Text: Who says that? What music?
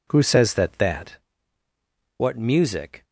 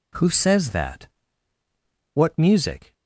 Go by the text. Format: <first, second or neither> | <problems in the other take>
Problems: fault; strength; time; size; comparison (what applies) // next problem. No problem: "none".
second | says "that" twice; at 0.7 s